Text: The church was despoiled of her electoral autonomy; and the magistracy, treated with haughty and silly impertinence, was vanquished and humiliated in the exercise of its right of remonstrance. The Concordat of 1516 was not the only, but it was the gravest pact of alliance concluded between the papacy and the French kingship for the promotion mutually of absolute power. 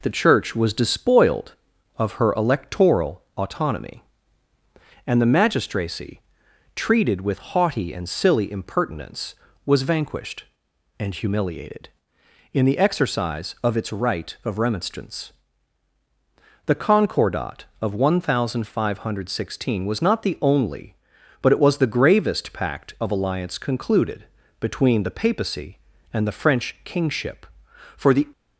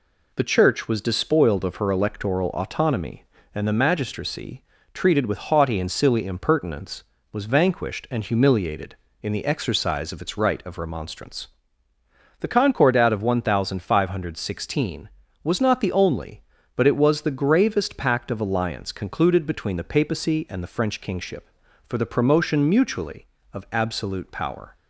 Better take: second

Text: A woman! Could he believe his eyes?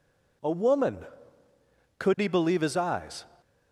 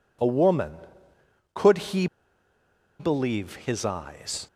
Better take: first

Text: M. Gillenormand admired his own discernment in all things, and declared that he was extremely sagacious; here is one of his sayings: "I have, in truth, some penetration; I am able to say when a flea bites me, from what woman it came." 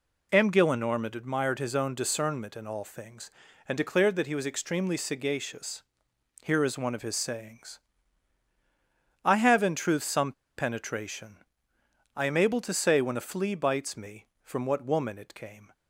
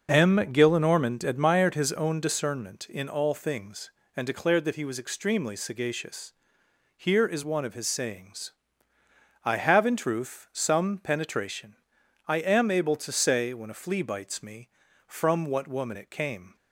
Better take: second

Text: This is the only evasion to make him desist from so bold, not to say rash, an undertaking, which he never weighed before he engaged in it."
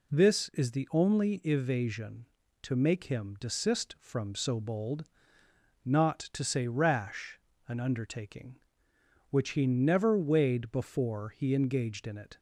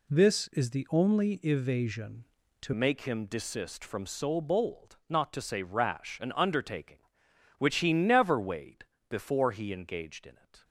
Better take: first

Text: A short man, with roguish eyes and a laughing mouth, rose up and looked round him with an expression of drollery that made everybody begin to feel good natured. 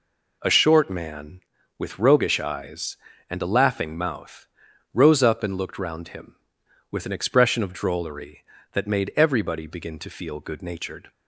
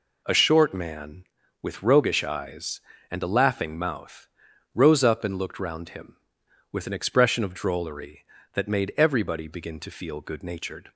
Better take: neither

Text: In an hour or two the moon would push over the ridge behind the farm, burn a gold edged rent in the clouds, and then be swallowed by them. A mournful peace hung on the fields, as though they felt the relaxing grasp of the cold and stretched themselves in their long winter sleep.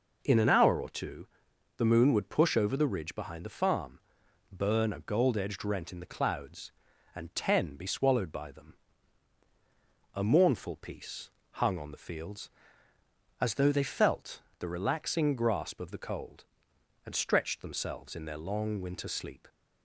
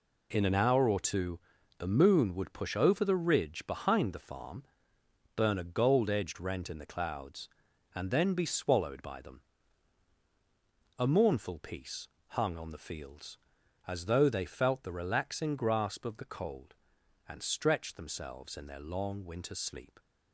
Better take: second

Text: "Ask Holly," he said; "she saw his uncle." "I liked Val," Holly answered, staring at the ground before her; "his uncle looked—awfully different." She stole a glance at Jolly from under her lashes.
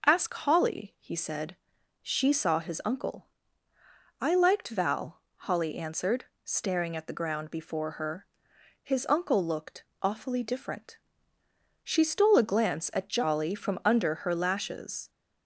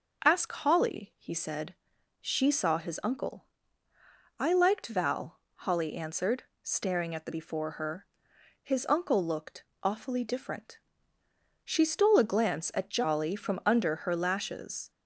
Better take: first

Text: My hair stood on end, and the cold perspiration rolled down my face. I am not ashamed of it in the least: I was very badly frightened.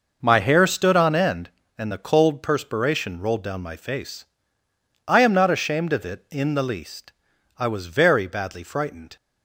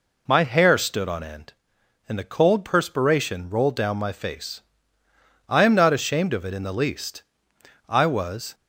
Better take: first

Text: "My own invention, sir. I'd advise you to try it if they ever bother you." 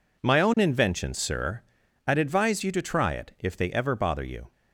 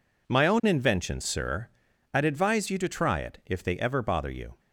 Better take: neither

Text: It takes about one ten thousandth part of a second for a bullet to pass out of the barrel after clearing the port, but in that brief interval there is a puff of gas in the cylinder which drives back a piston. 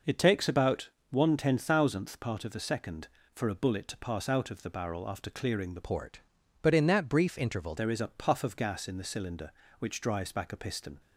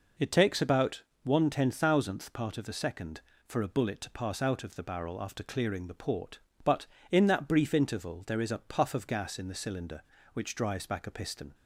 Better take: second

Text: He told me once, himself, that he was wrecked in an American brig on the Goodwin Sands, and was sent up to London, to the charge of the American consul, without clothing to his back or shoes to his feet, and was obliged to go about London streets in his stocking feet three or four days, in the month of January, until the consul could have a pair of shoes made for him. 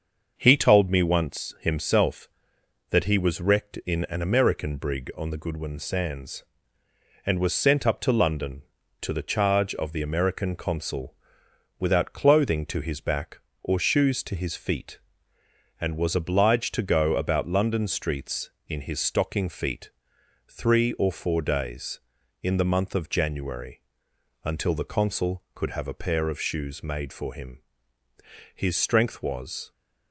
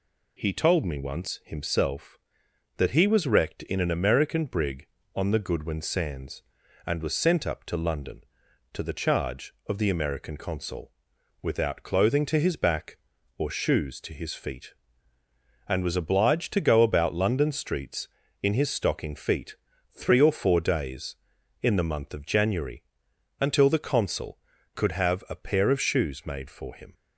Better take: second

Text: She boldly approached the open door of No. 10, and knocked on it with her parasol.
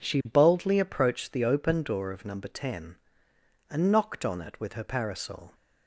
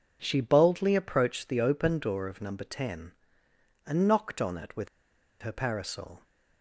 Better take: first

